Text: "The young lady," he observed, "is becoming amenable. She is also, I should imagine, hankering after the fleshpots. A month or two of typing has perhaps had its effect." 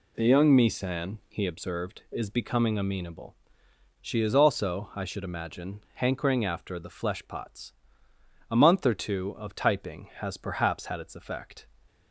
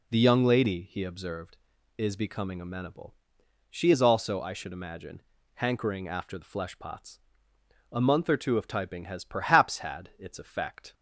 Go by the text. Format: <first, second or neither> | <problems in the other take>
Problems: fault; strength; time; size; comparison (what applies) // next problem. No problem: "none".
second | says "misan" for "lady"; at 0.5 s